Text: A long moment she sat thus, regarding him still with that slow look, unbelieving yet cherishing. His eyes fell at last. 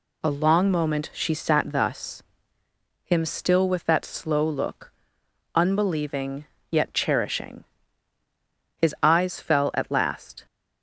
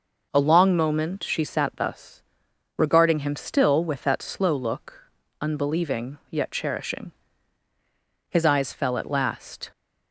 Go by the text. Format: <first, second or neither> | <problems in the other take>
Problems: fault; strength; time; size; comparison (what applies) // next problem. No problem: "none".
second | skips "regarding"; at 2.6 s // pauses between "unbelieving" and "yet"; slight; at 6.4 s; 0.24 s long